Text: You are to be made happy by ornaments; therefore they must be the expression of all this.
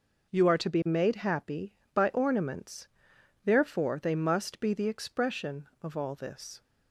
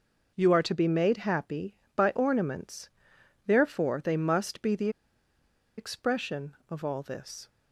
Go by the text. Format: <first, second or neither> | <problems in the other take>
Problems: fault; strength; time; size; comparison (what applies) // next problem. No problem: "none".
first | pauses between "the" and "expression"; noticeable; at 4.8 s; 0.88 s long